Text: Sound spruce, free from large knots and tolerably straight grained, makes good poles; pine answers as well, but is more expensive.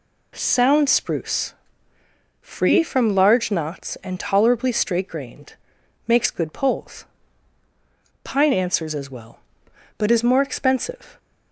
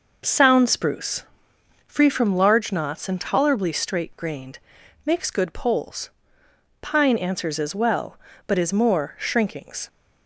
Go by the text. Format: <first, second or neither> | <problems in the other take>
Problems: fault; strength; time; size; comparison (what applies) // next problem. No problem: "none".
first | says "shrinkings" for "expensive"; at 9.1 s